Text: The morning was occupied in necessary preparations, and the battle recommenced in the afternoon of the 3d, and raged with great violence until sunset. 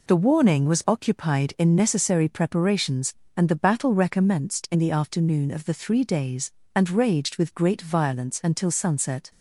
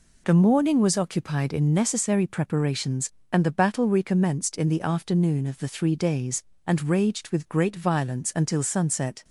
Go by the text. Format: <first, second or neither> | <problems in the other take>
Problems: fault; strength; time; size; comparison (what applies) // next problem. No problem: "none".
second | says "warning" for "morning"; at 0.1 s